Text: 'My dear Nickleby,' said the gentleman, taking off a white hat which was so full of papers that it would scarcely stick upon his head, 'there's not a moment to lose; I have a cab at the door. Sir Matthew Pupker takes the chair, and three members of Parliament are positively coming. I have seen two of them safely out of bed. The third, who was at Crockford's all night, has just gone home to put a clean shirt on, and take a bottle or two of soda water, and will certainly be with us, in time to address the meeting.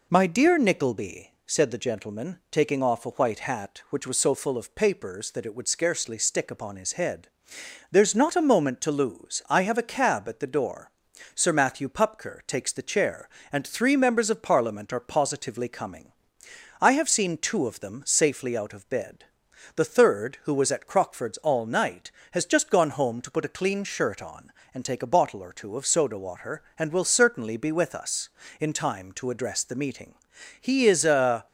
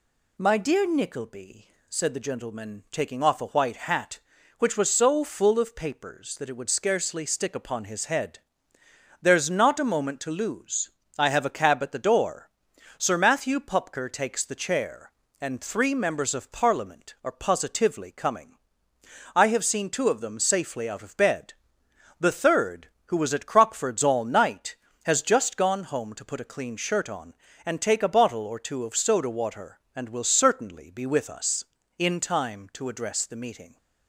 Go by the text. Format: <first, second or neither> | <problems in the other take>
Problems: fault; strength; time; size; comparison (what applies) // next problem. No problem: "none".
second | goes on to say "He is a"; noticeable; from 30.6 s on; 0.86 s long